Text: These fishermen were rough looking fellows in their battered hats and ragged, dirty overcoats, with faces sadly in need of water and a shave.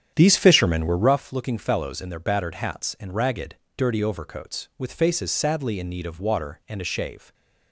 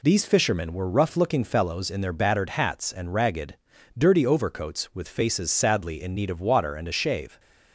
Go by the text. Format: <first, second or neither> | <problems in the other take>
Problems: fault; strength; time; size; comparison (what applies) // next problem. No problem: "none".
second | starts louder than the rest; strong; until 1.2 s; 9 dB // stays silent after the last word; slight; from 7.1 s on; 0.6 s long